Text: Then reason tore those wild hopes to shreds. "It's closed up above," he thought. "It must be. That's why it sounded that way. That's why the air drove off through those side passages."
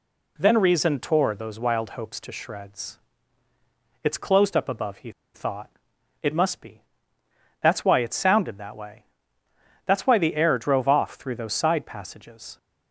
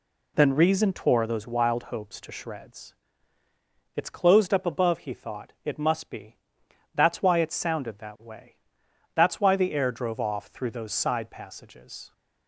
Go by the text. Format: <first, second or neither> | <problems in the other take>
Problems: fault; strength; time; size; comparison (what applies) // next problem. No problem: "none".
second | pauses between "he" and "thought"; slight; at 5.0 s; 0.24 s long